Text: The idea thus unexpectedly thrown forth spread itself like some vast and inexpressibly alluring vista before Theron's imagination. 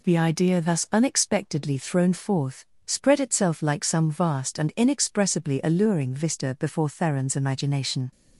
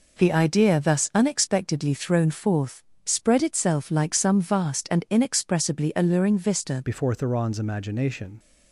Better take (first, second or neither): first